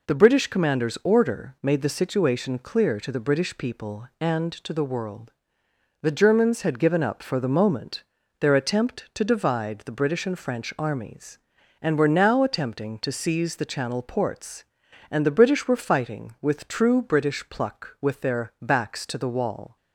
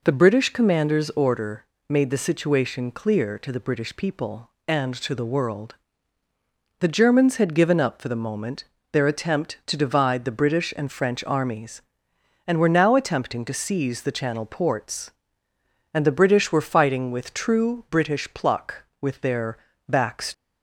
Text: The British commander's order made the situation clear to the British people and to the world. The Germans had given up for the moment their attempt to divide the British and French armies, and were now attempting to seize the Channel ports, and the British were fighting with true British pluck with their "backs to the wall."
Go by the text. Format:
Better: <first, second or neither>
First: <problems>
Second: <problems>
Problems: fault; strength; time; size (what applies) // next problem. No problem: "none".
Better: first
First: pauses between "moment" and "their"; slight; at 8.0 s; 0.34 s long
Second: pauses between "order" and "made"; slight; at 1.6 s; 0.24 s long // pauses between "moment" and "their"; slight; at 8.6 s; 0.26 s long // pauses between "their" and "backs"; slight; at 19.5 s; 0.32 s long // stops before "to the wall"; at 20.3 s